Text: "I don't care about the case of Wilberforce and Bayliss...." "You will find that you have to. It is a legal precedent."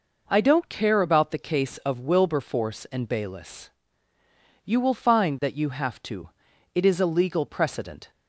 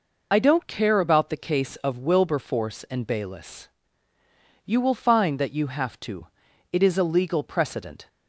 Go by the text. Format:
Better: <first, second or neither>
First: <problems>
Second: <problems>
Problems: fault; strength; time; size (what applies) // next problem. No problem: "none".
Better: first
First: none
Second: loses the start of "I"; at 0.3 s; 55 ms